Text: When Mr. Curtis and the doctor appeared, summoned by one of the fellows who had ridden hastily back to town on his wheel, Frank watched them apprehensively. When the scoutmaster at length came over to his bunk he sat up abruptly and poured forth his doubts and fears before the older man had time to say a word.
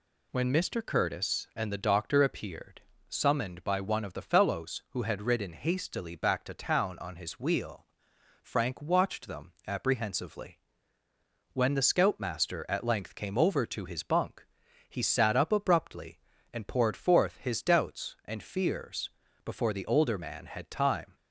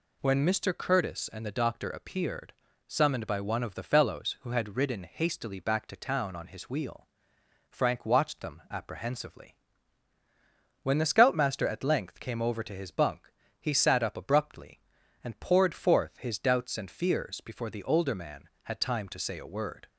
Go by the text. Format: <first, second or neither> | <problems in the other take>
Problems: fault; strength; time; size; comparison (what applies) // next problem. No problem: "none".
second | pauses between "bunk" and "he"; at 14.4 s; 0.42 s long; slight in the second // pauses between "fears" and "before"; slight; at 19.0 s; 0.34 s long // stops before "to say a word"; at 21.1 s